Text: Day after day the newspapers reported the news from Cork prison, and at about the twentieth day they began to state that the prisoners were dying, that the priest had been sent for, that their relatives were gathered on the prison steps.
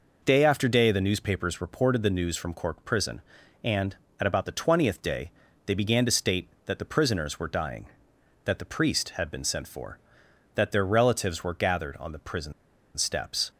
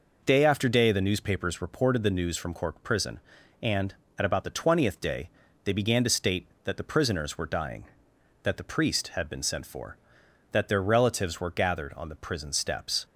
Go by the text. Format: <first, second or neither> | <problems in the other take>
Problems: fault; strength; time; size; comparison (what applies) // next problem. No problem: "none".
second | pauses between "day" and "they"; slight; at 5.3 s; 0.34 s long; slight in the second // pauses between "prison" and "steps"; at 12.5 s; 0.43 s long